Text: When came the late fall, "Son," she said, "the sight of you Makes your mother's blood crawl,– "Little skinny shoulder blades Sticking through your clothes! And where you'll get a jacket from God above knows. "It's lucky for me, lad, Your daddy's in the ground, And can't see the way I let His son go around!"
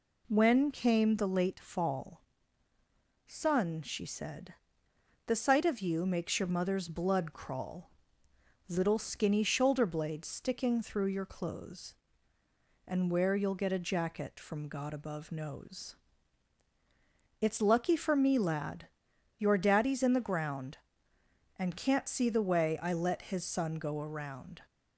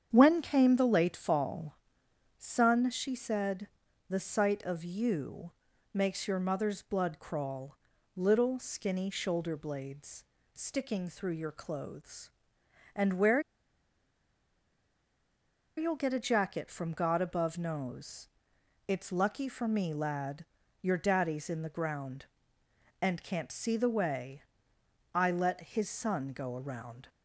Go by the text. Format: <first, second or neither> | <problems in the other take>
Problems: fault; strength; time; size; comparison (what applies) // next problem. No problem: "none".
first | starts louder than the rest; strong; until 1.1 s; 8 dB // pauses between "you" and "Makes"; at 5.5 s; 0.42 s long // pauses between "blades" and "Sticking"; slight; at 10.2 s; 0.28 s long // pauses between "where" and "you'll"; strong; at 13.3 s; 2.3 s long // pauses between "way" and "I"; noticeable; at 24.4 s; 0.70 s long